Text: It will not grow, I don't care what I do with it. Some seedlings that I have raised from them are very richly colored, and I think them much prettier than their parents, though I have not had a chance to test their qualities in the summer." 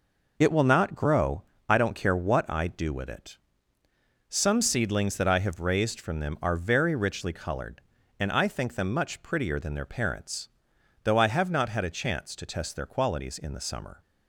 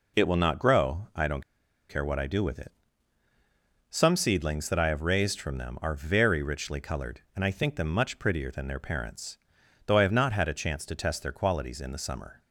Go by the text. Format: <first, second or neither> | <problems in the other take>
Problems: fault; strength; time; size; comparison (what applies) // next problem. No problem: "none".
first | pauses between "don't" and "care"; noticeable; at 1.4 s; 0.48 s long